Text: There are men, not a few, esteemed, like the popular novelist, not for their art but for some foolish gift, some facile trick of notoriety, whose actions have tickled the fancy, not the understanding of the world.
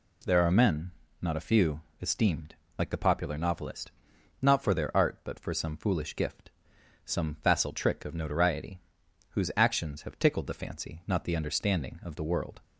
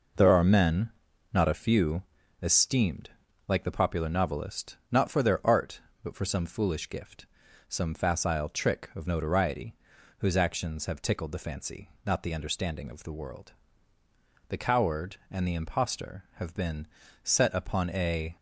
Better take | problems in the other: first | goes on to say "The coward and the impostor have been set upon a"; strong; from 14.4 s on; 3.8 s long

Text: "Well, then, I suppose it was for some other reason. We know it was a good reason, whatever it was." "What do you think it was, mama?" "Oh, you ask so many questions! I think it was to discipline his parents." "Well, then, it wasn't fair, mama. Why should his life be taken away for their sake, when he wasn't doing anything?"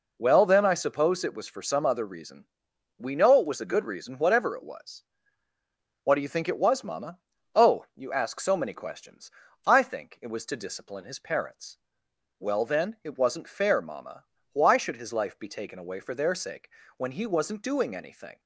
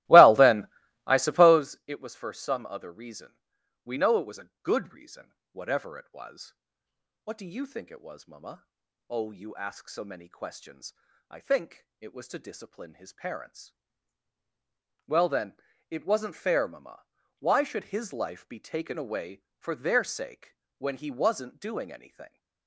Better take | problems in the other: first | starts louder than the rest; strong; until 1.7 s; 17.5 dB

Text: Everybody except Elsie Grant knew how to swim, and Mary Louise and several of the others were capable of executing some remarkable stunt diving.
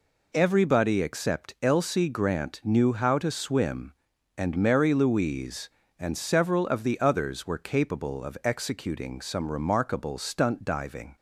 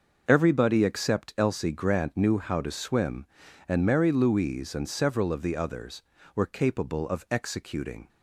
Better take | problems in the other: first | starts louder than the rest; noticeable; until 1.2 s; 6 dB // stops before "some remarkable stunt diving"; at 8.0 s

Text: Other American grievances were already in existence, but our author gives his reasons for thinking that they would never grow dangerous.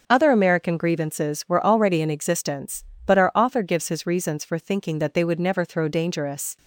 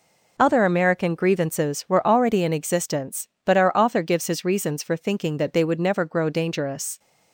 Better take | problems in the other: second | starts louder than the rest; until 1.0 s; 6.5 dB // says "throw" for "grow"; at 5.6 s

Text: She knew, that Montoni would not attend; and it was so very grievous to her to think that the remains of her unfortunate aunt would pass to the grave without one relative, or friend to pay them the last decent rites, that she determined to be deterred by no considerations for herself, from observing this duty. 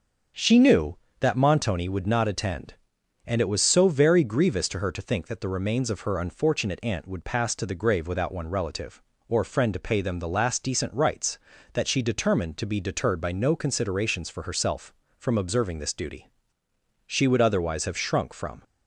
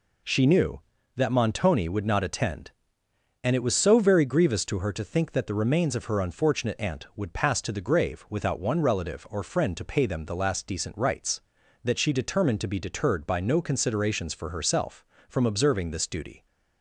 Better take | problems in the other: second | starts louder than the rest; until 1.6 s; 7 dB // goes on to say "She would otherwise have shrunk from"; from 17.0 s on; 1.5 s long

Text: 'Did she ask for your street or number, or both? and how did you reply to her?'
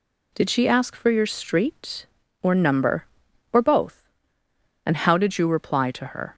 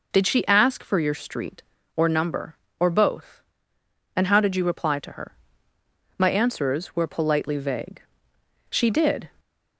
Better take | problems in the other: first | goes on to say "My answers were politely vague She did"; strong; from 6.1 s on; 3.1 s long

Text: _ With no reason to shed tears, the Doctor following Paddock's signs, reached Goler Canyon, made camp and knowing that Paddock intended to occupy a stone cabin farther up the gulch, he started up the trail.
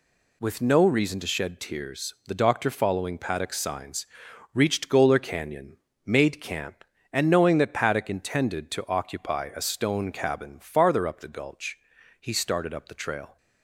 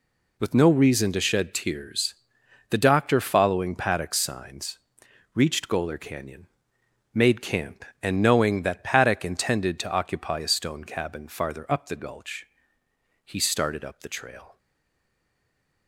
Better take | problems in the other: first | stays silent after the last word; noticeable; from 14.5 s on; 1.3 s long

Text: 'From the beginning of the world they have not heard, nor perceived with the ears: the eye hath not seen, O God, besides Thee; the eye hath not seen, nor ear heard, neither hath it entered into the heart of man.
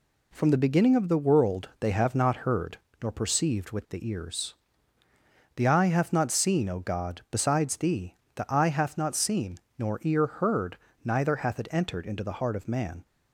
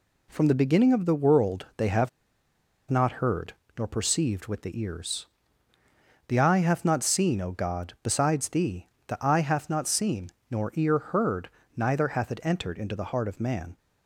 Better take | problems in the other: first | pauses between "have" and "not"; noticeable; at 2.0 s; 0.80 s long

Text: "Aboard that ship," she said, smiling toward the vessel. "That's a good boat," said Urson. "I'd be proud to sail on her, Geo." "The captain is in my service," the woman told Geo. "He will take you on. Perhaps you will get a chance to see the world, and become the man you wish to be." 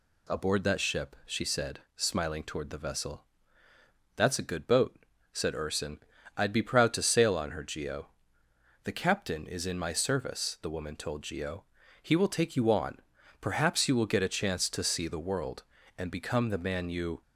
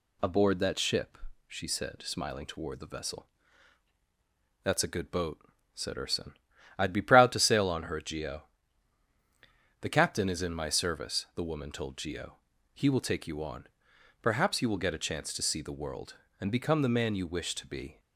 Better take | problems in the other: second | stops before "wish to be"; at 17.2 s

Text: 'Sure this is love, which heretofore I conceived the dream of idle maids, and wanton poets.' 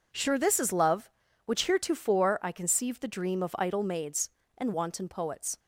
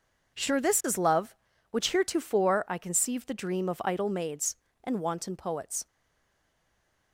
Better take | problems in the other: first | stays silent after the last word; noticeable; from 5.8 s on; 1.3 s long

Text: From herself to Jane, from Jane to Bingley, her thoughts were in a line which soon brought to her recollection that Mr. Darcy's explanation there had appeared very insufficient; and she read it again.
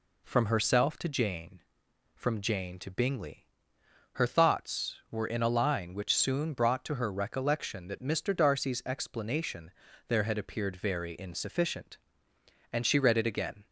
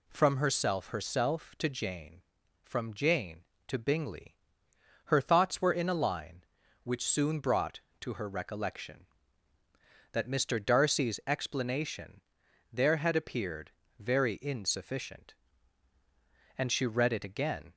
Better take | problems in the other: first | says "herself" twice; at 0.8 s // pauses between "explanation" and "there"; noticeable; at 12.2 s; 0.52 s long; also in the first // pauses between "appeared" and "very"; slight; at 13.7 s; 0.28 s long

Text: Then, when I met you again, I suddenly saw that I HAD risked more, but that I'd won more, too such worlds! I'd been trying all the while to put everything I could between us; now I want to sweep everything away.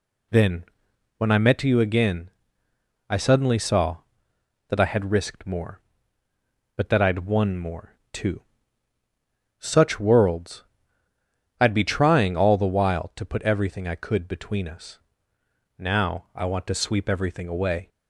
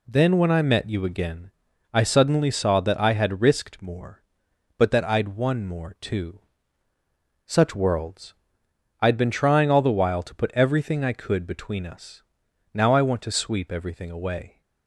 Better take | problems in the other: second | pauses between "too" and "such"; at 8.4 s; 1.1 s long; also in the second // says "be" for "been"; at 11.7 s

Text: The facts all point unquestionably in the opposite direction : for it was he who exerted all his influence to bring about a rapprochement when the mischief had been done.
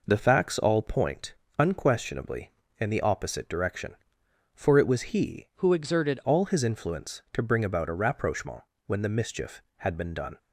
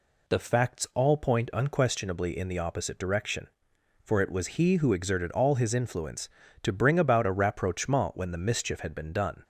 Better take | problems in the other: second | pauses between "point" and "unquestionably"; slight; at 1.3 s; 0.24 s long // changes voice from "who" to "exerted"; from 5.5 to 6.1 s; 0.6 s long // pauses between "rapprochement" and "when"; slight; at 8.6 s; 0.24 s long

